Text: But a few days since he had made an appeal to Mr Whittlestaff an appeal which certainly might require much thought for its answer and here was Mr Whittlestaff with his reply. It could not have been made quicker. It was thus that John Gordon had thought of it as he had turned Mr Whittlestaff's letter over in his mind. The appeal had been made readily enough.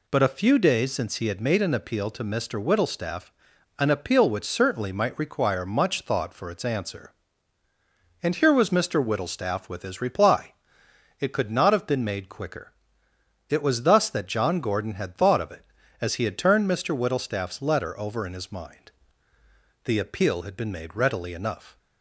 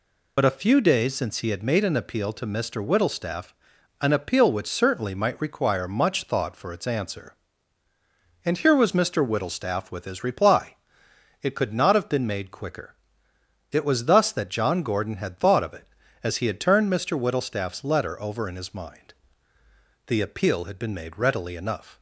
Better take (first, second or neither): first